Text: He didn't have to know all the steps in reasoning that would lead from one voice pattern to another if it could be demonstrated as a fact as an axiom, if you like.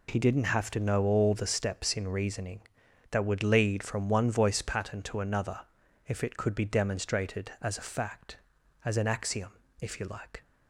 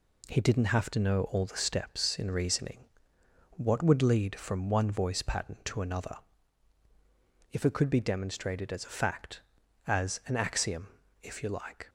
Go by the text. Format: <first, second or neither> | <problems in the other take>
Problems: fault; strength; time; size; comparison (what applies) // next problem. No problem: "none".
first | says "what" for "that"; at 3.5 s // pauses between "another" and "if"; strong; at 6.1 s; 1.3 s long; noticeable in the first